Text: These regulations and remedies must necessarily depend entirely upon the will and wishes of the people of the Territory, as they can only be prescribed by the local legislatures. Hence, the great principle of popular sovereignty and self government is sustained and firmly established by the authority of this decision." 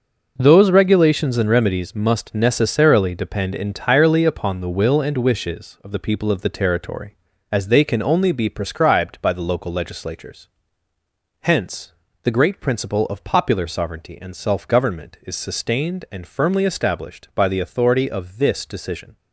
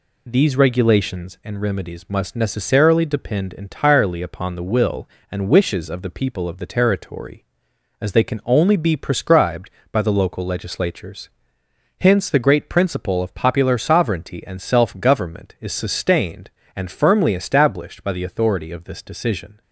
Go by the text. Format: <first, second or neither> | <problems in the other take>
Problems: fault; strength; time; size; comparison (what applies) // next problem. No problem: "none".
second | starts louder than the rest; noticeable; until 1.3 s; 6 dB // says "Those" for "These"; at 0.3 s